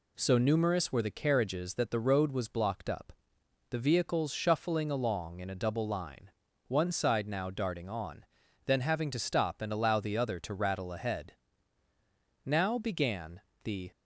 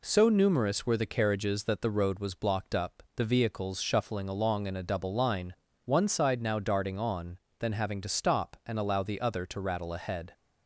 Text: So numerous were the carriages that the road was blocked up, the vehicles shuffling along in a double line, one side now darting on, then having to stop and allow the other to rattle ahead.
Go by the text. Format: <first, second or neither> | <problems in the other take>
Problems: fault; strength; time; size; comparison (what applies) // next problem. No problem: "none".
second | goes on to say "Now began the"; from 12.4 s on; 1.4 s long